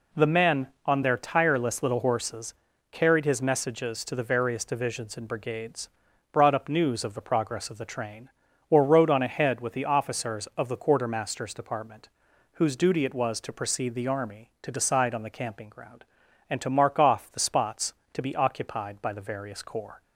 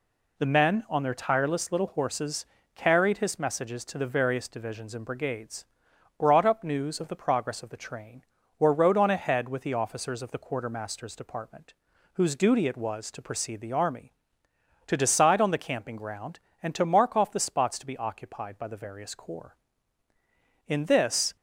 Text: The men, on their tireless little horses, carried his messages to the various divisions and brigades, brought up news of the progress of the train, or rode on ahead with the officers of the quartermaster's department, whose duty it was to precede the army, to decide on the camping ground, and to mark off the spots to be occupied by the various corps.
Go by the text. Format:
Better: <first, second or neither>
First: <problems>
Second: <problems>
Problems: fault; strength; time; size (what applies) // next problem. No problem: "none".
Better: first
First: none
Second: goes on to say "In this"; noticeable; from 20.6 s on; 0.68 s long